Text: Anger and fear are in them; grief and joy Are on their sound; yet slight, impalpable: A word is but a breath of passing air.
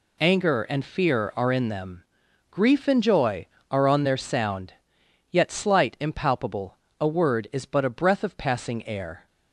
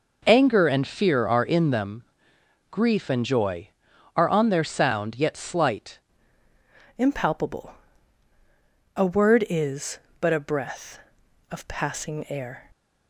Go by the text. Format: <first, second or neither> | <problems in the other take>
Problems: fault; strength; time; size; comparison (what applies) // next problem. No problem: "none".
first | changes voice at "impalpable"; from 6.9 s on; 5.7 s long